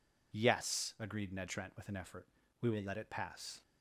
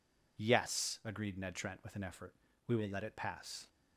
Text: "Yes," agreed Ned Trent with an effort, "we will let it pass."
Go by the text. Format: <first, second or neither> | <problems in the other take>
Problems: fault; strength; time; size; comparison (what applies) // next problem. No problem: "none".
neither | none